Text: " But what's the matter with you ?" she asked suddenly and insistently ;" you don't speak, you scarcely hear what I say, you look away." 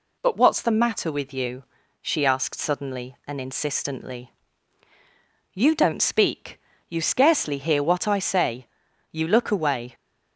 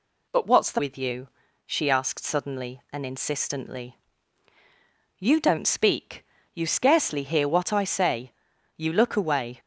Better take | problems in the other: first | skips "matter"; at 0.7 s

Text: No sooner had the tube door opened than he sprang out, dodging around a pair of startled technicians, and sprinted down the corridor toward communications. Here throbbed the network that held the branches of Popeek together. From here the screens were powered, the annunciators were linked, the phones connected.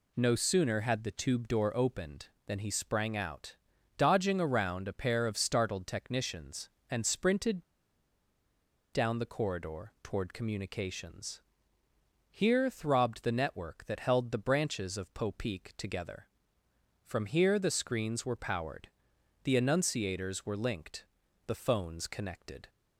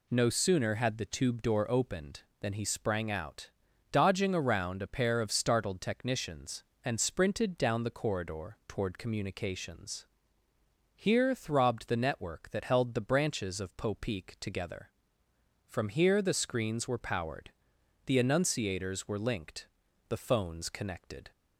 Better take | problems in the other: second | pauses between "sprinted" and "down"; strong; at 7.6 s; 1.2 s long

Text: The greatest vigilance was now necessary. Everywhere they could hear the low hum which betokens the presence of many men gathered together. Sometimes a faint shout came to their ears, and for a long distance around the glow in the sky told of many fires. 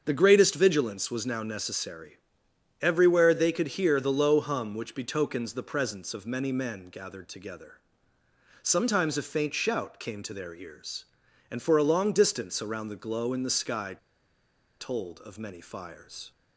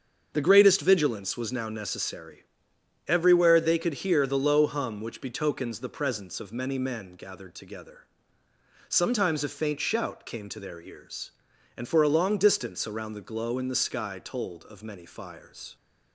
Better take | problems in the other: second | starts louder than the rest; until 1.0 s; 7 dB; also in the second // pauses between "sky" and "told"; noticeable; at 13.9 s; 0.85 s long

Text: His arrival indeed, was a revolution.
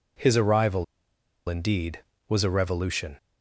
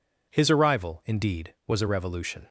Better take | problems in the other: second | pauses between "arrival" and "indeed"; noticeable; at 0.8 s; 0.64 s long

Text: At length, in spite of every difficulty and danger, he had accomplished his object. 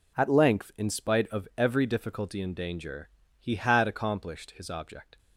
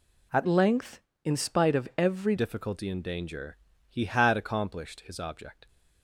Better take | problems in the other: first | changes voice from "length" to "every"; from 0.4 to 2.3 s; 1.9 s long

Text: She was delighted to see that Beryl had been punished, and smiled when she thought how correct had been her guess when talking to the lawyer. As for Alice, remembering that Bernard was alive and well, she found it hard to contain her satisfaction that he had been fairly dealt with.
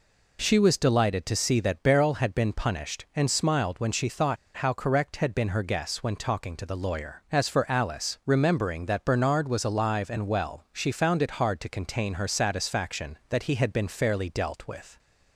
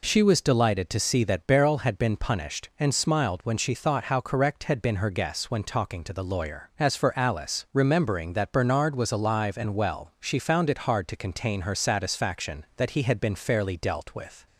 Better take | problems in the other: second | pauses between "thought" and "how"; slight; at 4.3 s; 0.20 s long

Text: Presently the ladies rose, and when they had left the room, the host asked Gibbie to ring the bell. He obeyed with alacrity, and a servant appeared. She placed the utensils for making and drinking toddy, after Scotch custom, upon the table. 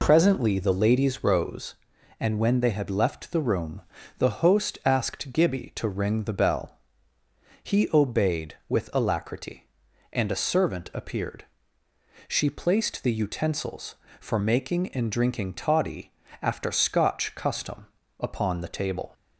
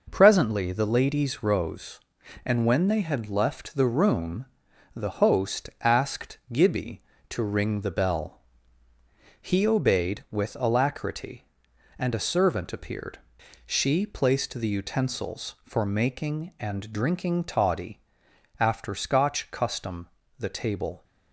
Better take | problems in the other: first | skips "upon"; at 20.2 s

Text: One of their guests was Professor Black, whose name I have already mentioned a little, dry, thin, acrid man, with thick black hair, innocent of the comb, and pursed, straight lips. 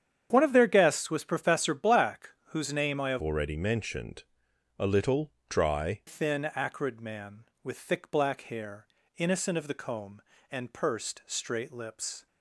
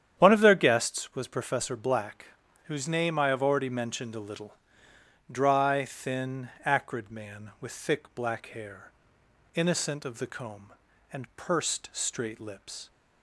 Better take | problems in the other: second | starts louder than the rest; strong; until 1.3 s; 8.5 dB; strong in the second // changes voice from "already" to "dry"; from 3.1 to 6.0 s; 2.9 s long // pauses between "mentioned" and "a"; noticeable; at 4.2 s; 0.56 s long

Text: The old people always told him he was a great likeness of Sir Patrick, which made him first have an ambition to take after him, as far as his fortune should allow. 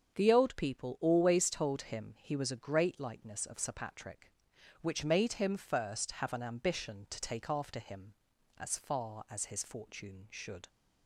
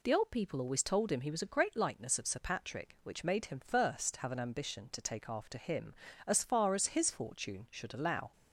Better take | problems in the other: second | starts louder than the rest; strong; until 1.1 s; 7 dB // stops before "allow"; at 10.6 s

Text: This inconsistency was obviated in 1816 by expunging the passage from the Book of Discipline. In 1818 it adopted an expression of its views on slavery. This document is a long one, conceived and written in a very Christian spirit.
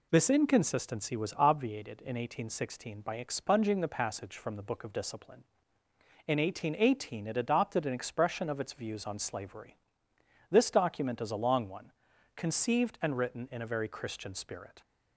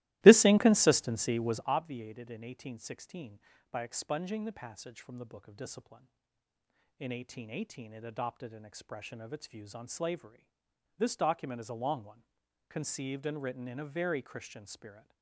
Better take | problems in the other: first | starts louder than the rest; strong; until 1.7 s; 18 dB

